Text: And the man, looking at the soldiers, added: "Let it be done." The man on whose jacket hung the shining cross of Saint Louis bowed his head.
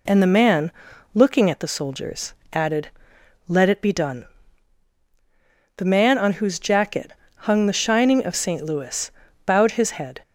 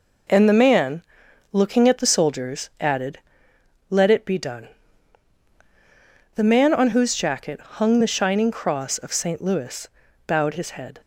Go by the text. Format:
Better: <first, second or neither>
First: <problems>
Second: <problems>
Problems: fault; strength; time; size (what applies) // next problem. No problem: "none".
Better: second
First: pauses between "jacket" and "hung"; slight; at 7.1 s; 0.26 s long // skips "cross"; at 8.2 s // pauses between "Louis" and "bowed"; slight; at 9.0 s; 0.36 s long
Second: pauses between "Louis" and "bowed"; at 9.8 s; 0.40 s long